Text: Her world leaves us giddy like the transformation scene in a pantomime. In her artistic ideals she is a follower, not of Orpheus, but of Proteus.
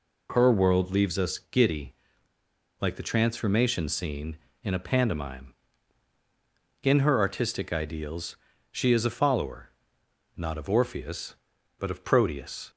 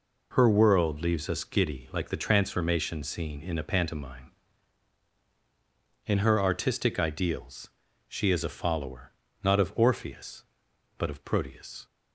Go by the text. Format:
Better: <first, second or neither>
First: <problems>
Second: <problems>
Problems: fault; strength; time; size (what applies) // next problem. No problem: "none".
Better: second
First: pauses between "giddy" and "like"; noticeable; at 1.9 s; 0.87 s long // pauses between "ideals" and "she"; slight; at 8.3 s; 0.34 s long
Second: pauses between "ideals" and "she"; at 7.6 s; 0.40 s long